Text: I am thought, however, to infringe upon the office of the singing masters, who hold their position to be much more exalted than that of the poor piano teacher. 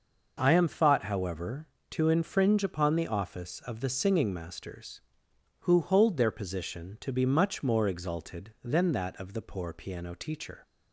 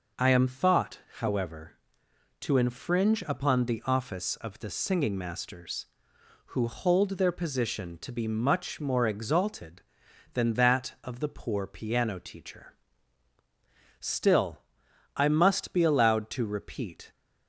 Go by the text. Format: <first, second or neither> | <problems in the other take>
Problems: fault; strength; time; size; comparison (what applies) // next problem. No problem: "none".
first | goes on to say "Still I must be allowed to repeat"; strong; from 13.9 s on; 3.1 s long